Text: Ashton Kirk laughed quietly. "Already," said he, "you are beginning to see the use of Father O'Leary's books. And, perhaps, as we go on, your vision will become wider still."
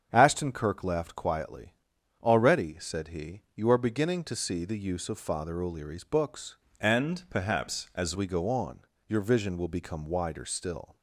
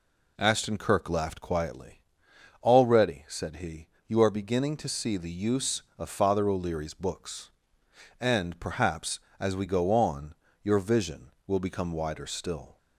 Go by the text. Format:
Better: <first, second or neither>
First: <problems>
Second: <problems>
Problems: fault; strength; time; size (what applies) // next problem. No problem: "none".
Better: second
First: starts louder than the rest; strong; until 1.1 s; 7.5 dB // changes voice from "And" to "as"; from 6.7 to 8.1 s; 1.4 s long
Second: none